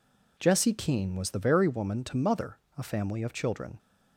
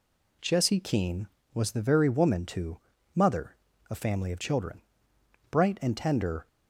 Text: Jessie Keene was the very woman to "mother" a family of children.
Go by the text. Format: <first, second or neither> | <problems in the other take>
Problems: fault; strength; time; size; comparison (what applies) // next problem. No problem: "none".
first | pauses between "to" and "mother"; slight; at 2.7 s; 0.36 s long // pauses between "mother" and "a"; slight; at 3.5 s; 0.34 s long; slight in the first // goes on to say "Bright and tender"; noticeable; from 5.4 s on; 0.98 s long